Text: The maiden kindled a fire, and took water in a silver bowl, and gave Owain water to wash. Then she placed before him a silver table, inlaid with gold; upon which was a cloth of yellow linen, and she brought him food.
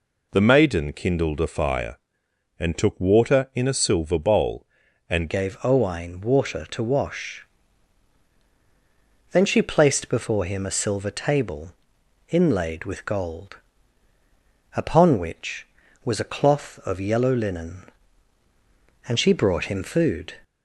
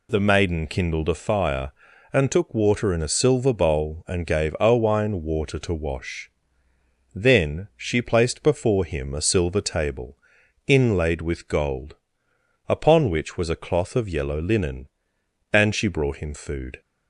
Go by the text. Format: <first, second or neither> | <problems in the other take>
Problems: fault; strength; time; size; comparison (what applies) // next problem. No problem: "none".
second | changes voice at "gave"; from 5.2 s on; 15.1 s long